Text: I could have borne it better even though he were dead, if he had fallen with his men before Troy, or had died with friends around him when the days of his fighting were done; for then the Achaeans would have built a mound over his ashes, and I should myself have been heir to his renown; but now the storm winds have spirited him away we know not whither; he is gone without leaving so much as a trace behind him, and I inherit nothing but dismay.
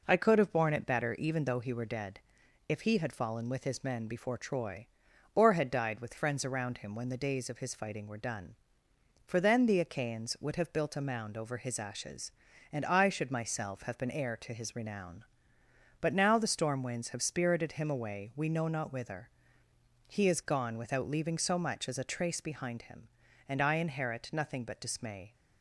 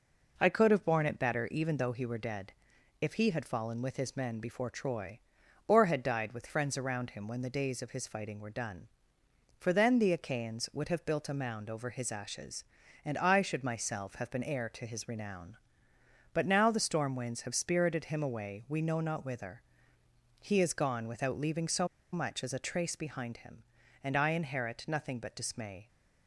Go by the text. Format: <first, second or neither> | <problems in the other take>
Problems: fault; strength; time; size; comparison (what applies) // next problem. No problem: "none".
first | pauses between "so" and "much"; slight; at 21.8 s; 0.26 s long